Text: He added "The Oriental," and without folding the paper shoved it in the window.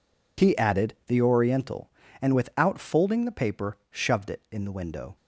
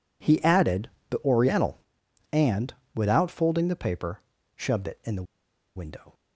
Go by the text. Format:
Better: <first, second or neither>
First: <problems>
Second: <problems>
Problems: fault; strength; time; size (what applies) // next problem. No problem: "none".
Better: first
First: none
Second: pauses between "added" and "The"; slight; at 0.8 s; 0.22 s long // pauses between "and" and "without"; slight; at 2.7 s; 0.22 s long // pauses between "paper" and "shoved"; slight; at 4.1 s; 0.36 s long // pauses between "the" and "window"; noticeable; at 5.2 s; 0.52 s long